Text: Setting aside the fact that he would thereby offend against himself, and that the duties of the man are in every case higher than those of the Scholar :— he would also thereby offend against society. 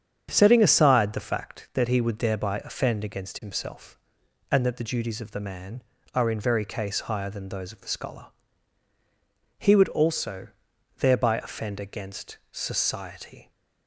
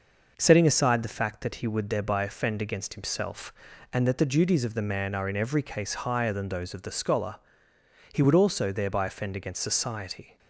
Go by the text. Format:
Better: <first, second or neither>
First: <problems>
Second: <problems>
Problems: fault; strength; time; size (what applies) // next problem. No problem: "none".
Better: second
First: starts louder than the rest; strong; until 1.3 s; 8 dB // says "very" for "every"; at 6.4 s // pauses between "also" and "thereby"; noticeable; at 10.4 s; 0.48 s long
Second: none